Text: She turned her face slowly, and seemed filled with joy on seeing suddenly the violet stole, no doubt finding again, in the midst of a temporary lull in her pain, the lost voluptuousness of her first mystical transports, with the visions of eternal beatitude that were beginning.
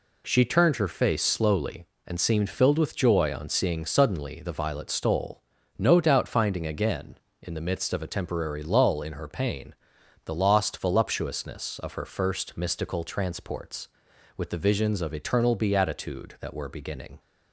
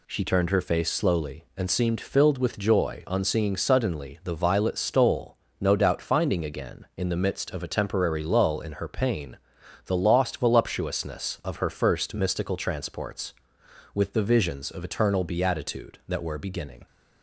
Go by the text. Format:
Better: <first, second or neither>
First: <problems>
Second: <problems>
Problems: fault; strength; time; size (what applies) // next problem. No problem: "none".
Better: neither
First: none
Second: none